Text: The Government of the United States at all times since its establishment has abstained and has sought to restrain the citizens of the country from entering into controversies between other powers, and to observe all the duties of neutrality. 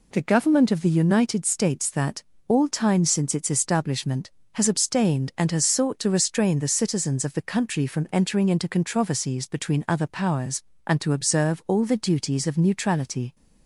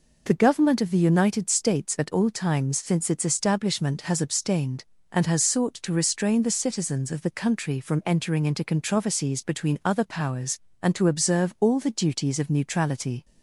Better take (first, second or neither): second